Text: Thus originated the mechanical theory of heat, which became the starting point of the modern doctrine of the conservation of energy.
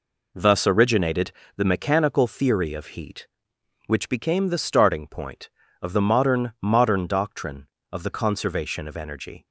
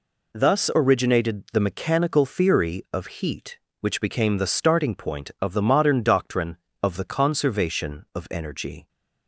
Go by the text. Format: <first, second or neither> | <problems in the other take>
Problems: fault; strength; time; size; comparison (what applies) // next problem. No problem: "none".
second | pauses between "originated" and "the"; slight; at 1.3 s; 0.24 s long // says "modern" twice; at 6.6 s